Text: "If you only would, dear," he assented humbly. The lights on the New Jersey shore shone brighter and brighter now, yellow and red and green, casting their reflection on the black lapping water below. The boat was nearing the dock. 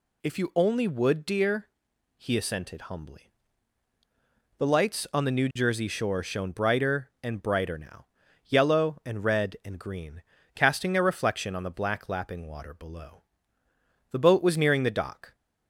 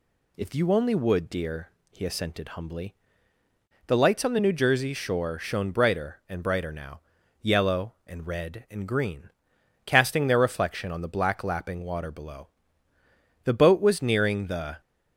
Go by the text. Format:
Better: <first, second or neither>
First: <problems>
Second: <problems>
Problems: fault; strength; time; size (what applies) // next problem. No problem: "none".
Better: first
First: none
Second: stops before "dock"; at 14.8 s